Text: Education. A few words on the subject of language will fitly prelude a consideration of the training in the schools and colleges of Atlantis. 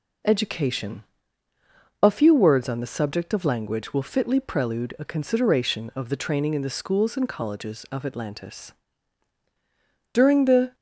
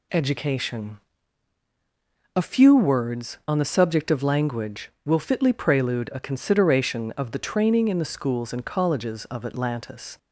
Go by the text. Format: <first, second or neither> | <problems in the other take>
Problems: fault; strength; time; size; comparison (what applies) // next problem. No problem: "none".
second | goes on to say "During the"; noticeable; from 10.1 s on; 0.62 s long